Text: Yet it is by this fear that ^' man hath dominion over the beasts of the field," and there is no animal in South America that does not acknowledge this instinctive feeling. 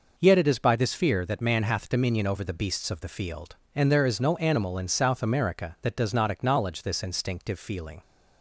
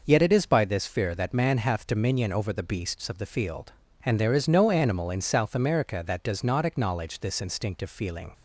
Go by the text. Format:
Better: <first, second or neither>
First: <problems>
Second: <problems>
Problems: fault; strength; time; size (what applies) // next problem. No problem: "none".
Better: neither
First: none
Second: none